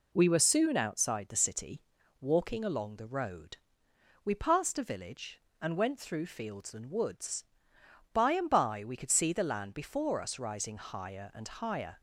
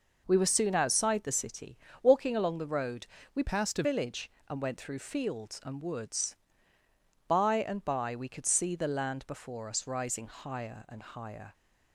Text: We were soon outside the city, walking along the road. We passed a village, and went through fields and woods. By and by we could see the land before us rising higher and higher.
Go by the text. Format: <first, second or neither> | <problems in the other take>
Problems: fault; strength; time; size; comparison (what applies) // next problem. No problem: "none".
first | changes voice from "passed" to "a"; from 3.4 to 3.8 s; 0.4 s long